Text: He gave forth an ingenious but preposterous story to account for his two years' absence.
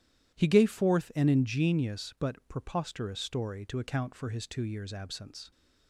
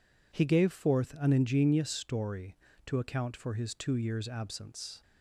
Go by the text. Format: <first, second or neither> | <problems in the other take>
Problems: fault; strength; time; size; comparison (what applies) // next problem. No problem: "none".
first | skips "but preposterous"; at 1.8 s